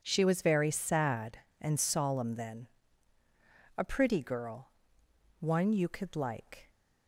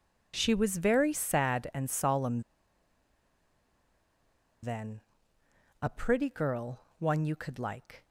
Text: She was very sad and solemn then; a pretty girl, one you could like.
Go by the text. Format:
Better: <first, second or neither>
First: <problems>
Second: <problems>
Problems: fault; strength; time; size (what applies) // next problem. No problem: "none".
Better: first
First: none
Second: pauses between "solemn" and "then"; strong; at 2.4 s; 2.2 s long